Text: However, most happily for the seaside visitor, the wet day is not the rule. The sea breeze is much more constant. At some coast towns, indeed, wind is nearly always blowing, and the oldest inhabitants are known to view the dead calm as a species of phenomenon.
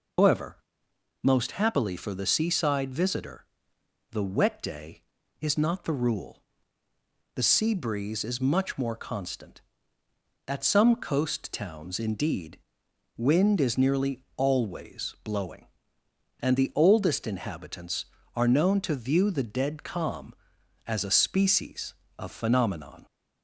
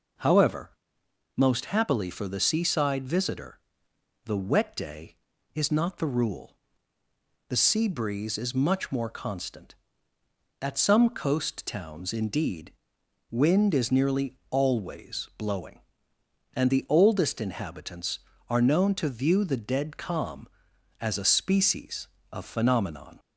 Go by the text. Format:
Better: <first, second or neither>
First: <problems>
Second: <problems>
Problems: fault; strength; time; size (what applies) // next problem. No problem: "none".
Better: second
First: loses the start of "However"; at 0.1 s; 150 ms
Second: none